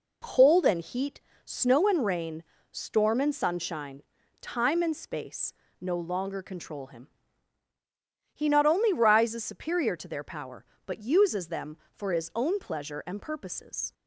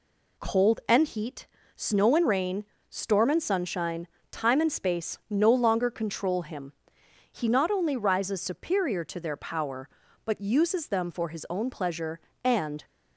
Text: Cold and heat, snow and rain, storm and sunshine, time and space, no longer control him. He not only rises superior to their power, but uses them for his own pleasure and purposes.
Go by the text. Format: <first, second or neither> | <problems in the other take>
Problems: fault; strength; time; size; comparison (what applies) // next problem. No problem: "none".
first | stops before "purposes"; at 12.8 s